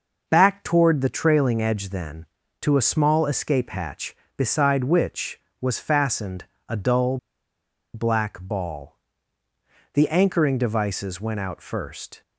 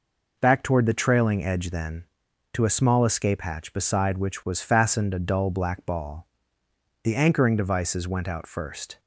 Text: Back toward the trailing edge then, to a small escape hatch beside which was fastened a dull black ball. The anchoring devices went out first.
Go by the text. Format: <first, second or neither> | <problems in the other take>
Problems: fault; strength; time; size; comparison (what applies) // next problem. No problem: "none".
second | pauses between "fastened" and "a"; slight; at 6.4 s; 0.24 s long // pauses between "dull" and "black"; noticeable; at 7.1 s; 0.77 s long